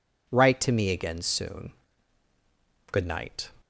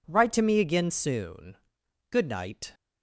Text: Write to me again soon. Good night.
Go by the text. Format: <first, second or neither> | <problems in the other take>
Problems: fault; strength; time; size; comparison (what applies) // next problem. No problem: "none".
neither | none